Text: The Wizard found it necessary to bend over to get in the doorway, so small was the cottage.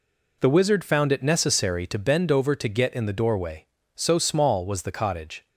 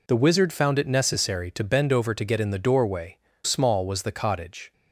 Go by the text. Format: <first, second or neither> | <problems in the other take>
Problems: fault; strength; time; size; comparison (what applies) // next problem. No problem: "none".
first | skips "so"; at 3.3 s